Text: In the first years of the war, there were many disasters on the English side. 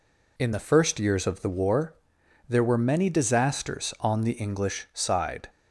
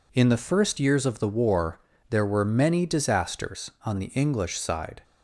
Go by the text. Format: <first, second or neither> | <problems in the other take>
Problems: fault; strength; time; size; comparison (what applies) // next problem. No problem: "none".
neither | none